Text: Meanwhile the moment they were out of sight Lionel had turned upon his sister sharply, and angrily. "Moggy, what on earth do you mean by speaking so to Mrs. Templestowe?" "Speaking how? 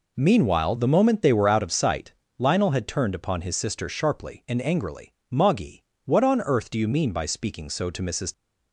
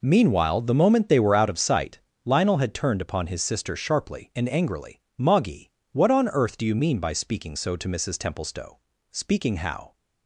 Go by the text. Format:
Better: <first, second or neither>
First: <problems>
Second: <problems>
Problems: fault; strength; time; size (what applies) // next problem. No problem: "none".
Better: second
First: pauses between "sight" and "Lionel"; slight; at 2.1 s; 0.26 s long // stops before "Templestowe Speaking how"; at 8.3 s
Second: pauses between "sight" and "Lionel"; slight; at 2.0 s; 0.26 s long